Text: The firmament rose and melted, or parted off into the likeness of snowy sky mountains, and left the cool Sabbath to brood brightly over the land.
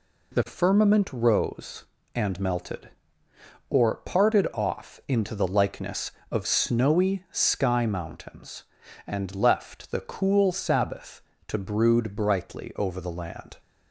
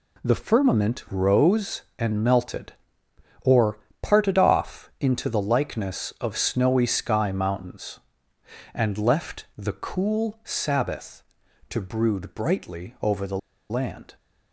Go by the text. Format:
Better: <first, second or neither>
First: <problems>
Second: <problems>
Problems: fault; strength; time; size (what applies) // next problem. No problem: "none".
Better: first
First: none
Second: pauses between "or" and "parted"; slight; at 3.7 s; 0.22 s long // pauses between "the" and "land"; slight; at 13.3 s; 0.30 s long